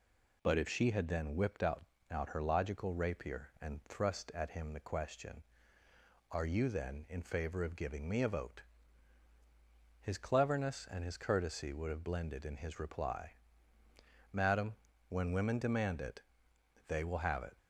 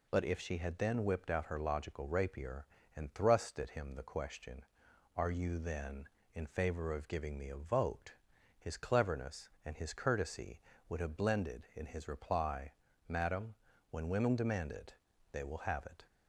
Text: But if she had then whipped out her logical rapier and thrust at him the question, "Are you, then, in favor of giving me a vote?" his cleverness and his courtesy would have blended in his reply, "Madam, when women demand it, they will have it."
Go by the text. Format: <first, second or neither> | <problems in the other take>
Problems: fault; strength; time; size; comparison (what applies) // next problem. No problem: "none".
second | says "out" twice; at 2.1 s